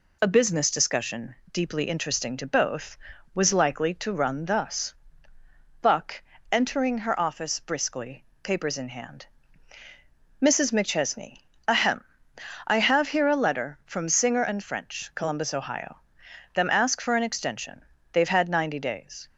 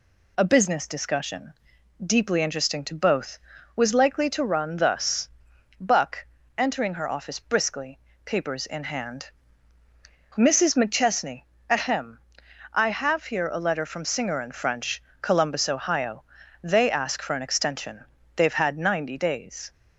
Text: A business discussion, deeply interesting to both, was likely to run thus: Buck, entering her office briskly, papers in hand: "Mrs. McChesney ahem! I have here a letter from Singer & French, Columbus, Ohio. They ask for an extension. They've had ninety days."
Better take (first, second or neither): second